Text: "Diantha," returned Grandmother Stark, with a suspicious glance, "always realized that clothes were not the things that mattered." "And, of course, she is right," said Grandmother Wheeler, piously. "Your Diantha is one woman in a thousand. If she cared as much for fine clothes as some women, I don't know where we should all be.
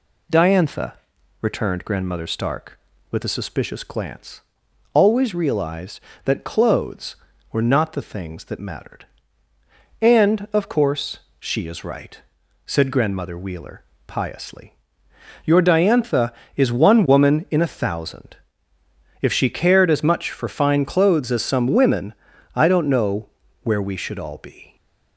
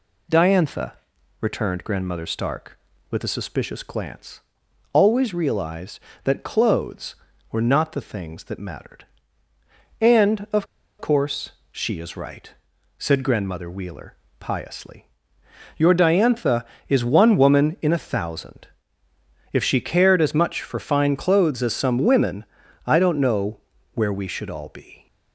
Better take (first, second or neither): first